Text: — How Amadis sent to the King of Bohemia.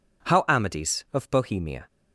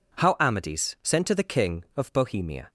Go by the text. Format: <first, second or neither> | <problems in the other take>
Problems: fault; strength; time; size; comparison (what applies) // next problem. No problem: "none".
second | skips "sent to the King"; at 1.0 s